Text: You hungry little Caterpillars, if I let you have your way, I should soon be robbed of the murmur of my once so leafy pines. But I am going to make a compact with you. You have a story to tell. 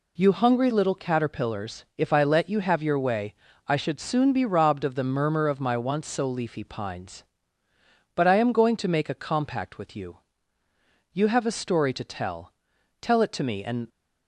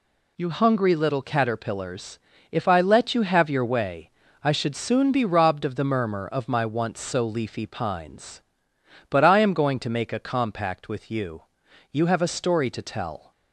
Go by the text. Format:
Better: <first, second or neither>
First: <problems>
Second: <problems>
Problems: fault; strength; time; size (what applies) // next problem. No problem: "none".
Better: second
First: goes on to say "Tell it to me and"; noticeable; from 13.0 s on; 0.86 s long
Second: none